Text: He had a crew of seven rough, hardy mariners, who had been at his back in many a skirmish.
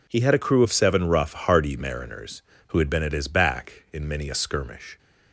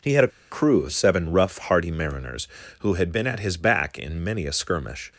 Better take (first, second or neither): first